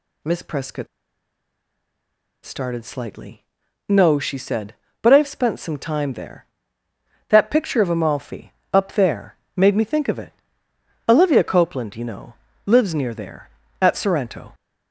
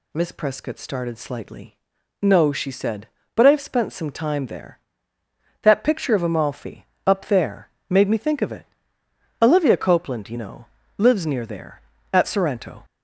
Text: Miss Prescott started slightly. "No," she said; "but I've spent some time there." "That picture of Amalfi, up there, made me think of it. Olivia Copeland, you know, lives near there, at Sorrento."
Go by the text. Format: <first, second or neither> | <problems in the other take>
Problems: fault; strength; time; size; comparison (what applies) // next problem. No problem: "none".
second | pauses between "Prescott" and "started"; strong; at 0.8 s; 1.5 s long